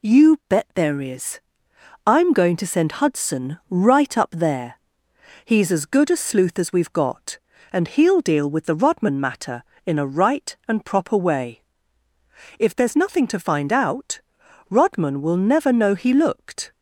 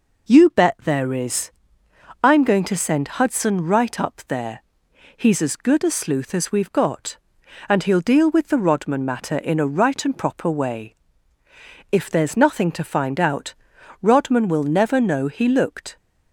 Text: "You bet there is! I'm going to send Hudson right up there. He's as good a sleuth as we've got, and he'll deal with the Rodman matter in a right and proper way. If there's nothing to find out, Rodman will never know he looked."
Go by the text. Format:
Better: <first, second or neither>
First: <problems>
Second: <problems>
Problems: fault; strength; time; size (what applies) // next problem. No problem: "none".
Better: neither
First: none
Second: none